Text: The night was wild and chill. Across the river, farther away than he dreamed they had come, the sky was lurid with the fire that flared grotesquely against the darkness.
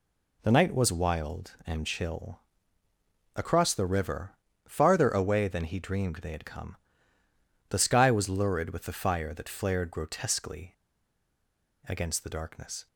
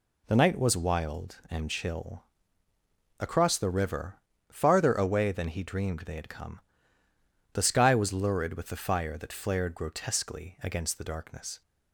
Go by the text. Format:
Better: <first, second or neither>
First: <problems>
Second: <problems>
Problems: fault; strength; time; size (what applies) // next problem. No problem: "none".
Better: second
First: pauses between "grotesquely" and "against"; at 10.7 s; 1.1 s long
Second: none